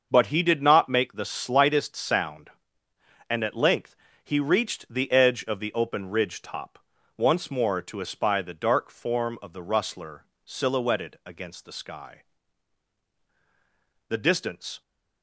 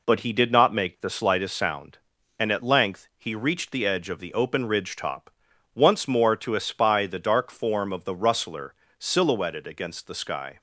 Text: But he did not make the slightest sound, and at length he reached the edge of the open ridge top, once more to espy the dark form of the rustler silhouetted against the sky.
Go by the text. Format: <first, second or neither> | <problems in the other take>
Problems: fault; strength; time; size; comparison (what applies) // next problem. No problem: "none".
second | starts louder than the rest; until 1.1 s; 6.5 dB // pauses between "length" and "he"; slight; at 3.9 s; 0.26 s long // pauses between "rustler" and "silhouetted"; slight; at 10.2 s; 0.18 s long; slight in the second // goes on to say "The distance"; noticeable; from 14.0 s on; 0.72 s long